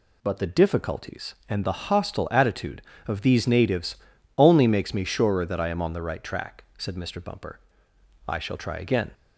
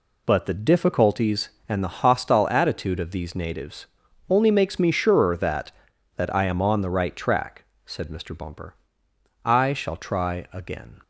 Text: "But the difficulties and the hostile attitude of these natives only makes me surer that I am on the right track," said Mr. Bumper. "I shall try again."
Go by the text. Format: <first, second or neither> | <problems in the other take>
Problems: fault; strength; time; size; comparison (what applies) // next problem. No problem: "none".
first | pauses between "natives" and "only"; at 3.8 s; 0.42 s long; also in the first // says "that" twice; at 6.1 s